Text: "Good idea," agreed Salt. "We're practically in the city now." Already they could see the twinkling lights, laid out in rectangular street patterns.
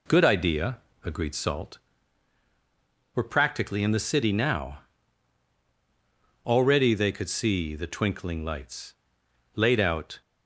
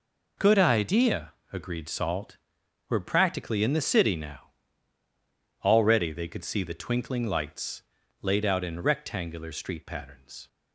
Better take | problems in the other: second | stops before "in rectangular street patterns"; at 10.2 s

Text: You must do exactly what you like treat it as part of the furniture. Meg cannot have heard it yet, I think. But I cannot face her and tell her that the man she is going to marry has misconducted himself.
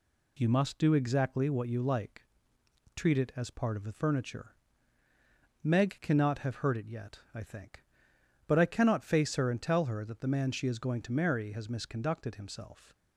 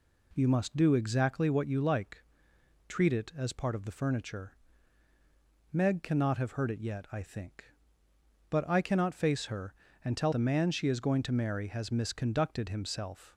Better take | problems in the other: first | pauses between "like" and "treat"; noticeable; at 2.2 s; 0.66 s long; noticeable in the first // skips "her that"; at 10.3 s

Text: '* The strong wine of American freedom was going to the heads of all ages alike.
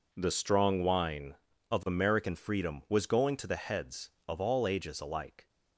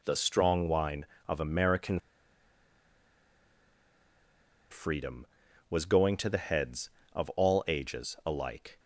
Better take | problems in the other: first | pauses between "American" and "freedom"; strong; at 2.0 s; 2.7 s long

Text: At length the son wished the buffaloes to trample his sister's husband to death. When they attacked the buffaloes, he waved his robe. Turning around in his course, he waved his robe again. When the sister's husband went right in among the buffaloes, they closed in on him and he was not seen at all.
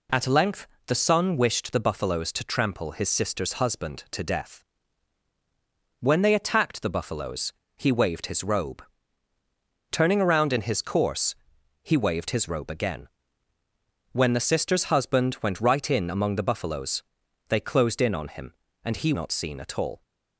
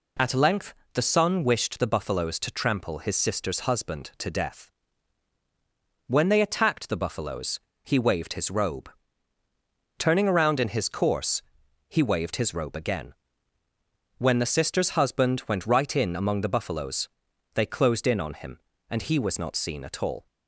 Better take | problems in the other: second | pauses between "length" and "the"; slight; at 0.6 s; 0.20 s long; slight in the second // skips "was"; at 19.1 s

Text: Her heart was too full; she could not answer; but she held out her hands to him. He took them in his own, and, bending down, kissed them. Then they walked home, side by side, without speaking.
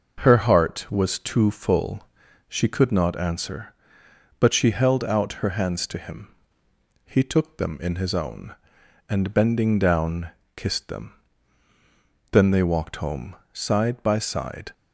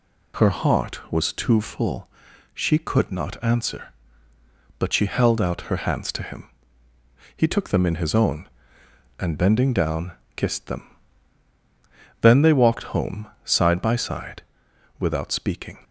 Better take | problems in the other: second | stops before "without speaking"; at 14.7 s

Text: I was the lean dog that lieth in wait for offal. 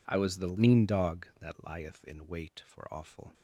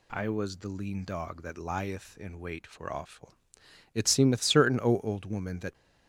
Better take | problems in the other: first | goes on to say "It seemeth certain O old woman that"; strong; from 3.9 s on; 1.7 s long

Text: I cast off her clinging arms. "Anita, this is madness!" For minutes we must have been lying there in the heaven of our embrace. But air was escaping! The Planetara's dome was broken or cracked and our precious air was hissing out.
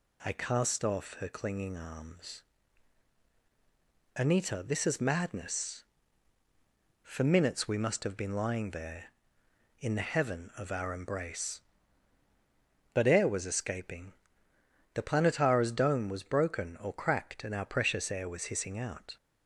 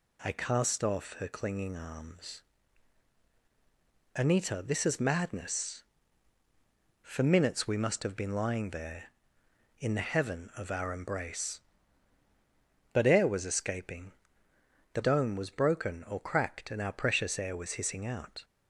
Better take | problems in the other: first | skips "Planetara's"; at 15.0 s

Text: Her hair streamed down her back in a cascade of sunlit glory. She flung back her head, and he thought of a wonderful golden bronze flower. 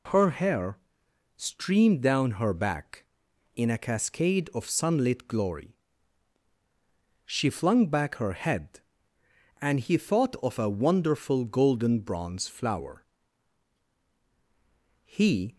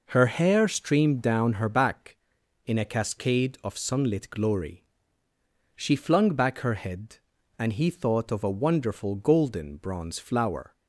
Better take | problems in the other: second | pauses between "hair" and "streamed"; noticeable; at 0.7 s; 0.58 s long // goes on to say "He"; from 15.0 s on; 0.52 s long

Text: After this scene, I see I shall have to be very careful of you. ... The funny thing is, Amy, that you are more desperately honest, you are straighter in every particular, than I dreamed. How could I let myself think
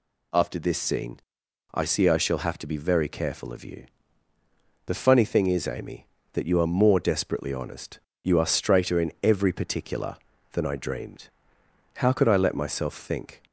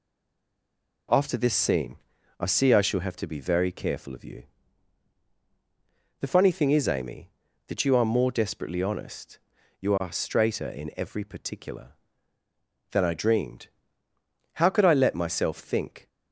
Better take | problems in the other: first | stays silent before the first word; until 1.0 s; 1.0 s long

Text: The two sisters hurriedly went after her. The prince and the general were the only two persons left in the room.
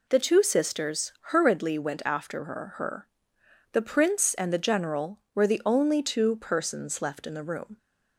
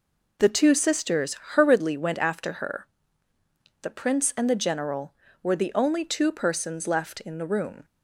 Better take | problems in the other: second | pauses between "sisters" and "hurriedly"; slight; at 1.1 s; 0.18 s long; slight in the second // says "her" twice; at 2.7 s

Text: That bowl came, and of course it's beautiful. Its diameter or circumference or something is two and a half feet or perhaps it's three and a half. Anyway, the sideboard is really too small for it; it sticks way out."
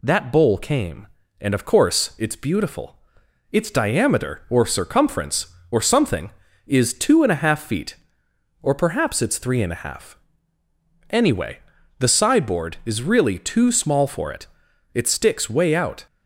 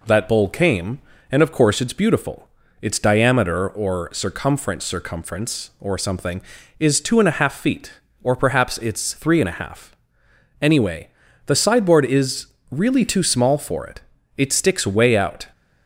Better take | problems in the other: first | says "circumference" twice; at 4.8 s // pauses between "is" and "really"; slight; at 12.4 s; 0.24 s long

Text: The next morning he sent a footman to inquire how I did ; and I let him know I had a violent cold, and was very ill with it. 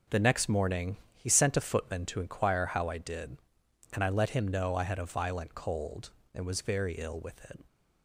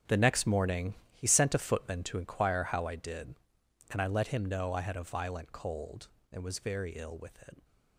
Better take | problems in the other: first | gets quieter; strong; throughout; 13 dB // pauses between "morning" and "he"; slight; at 0.9 s; 0.18 s long; slight in the first

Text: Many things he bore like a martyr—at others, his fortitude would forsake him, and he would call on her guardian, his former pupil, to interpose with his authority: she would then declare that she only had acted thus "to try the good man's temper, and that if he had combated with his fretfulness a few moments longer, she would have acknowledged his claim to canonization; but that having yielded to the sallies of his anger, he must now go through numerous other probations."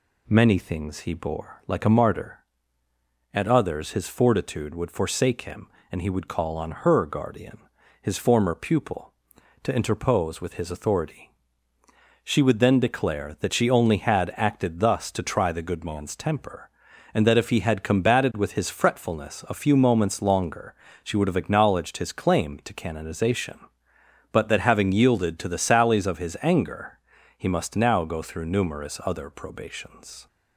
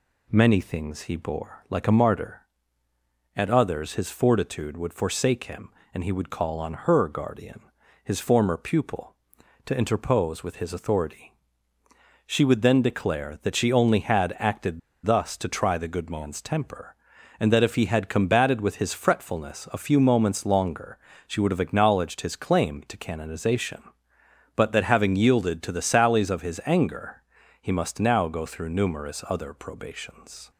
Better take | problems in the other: first | pauses between "acted" and "thus"; slight; at 14.7 s; 0.26 s long

